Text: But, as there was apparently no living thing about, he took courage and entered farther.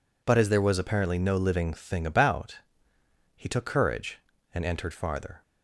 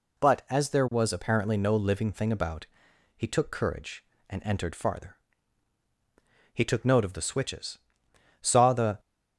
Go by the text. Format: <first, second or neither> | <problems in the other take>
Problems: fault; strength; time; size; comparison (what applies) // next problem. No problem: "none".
first | goes on to say "He took note of the switches saw the"; strong; from 6.5 s on; 2.4 s long